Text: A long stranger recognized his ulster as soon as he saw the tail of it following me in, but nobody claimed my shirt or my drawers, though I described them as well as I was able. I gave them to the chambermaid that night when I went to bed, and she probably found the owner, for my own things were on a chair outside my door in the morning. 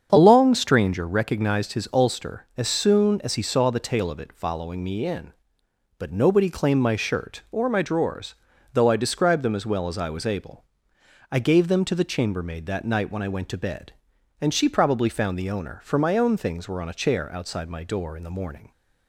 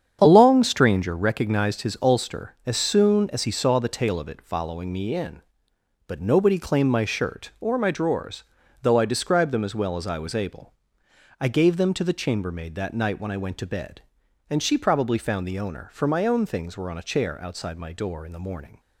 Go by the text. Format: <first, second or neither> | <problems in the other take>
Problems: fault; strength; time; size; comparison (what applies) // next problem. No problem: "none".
first | gets quieter; strong; throughout; 10 dB // starts louder than the rest; strong; until 1.2 s; 8 dB; strong in the first